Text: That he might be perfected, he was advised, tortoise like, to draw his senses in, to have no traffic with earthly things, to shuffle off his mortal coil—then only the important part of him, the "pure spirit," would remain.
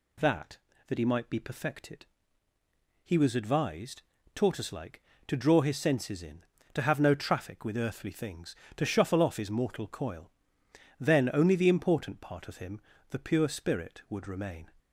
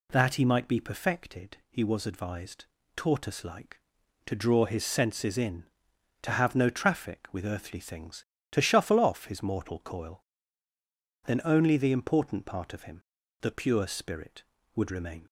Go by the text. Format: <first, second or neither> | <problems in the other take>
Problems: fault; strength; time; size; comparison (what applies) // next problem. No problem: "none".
second | says "That" twice; at 0.8 s